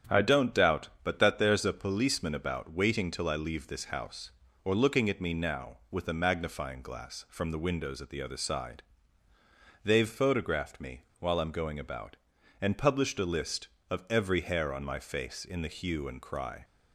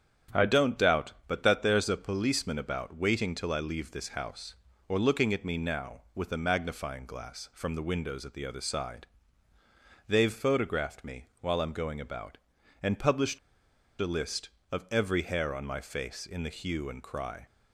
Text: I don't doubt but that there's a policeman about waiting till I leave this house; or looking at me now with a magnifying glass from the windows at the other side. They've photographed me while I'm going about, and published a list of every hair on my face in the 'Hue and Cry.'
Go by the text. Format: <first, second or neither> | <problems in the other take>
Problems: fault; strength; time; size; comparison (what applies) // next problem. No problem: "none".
first | starts louder than the rest; strong; until 1.4 s; 8 dB; strong in the first // pauses between "me" and "while"; slight; at 11.2 s; 0.16 s long; slight in the first // pauses between "published" and "a"; noticeable; at 13.3 s; 0.62 s long